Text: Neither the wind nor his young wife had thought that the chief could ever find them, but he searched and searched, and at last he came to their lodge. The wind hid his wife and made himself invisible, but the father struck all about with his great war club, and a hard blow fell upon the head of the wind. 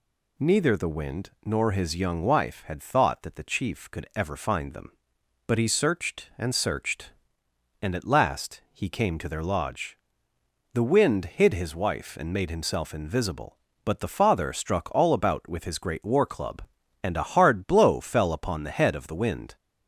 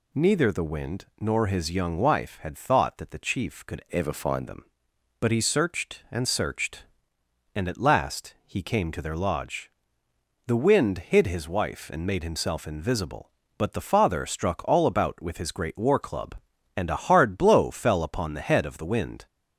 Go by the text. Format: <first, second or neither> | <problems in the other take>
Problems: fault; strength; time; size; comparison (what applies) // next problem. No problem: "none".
first | changes voice from "ever" to "find"; from 3.9 to 4.4 s; 0.5 s long